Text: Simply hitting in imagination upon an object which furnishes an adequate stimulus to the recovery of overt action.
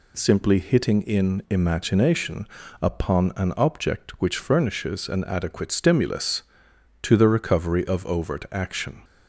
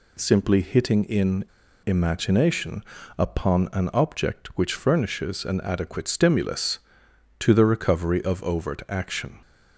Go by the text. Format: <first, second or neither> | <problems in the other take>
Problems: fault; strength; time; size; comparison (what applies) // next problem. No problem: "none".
first | pauses between "in" and "imagination"; at 1.4 s; 0.41 s long // pauses between "imagination" and "upon"; slight; at 2.8 s; 0.34 s long; slight in the first